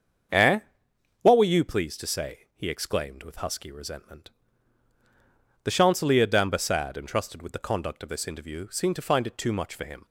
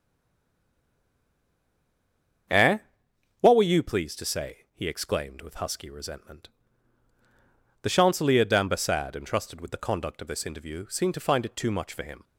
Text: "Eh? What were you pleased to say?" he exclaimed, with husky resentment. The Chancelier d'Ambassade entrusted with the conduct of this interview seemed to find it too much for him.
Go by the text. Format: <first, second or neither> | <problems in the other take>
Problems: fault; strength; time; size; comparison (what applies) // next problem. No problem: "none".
first | stays silent before the first word; until 2.4 s; 2.4 s long // starts louder than the rest; until 4.1 s; 7 dB; also in the first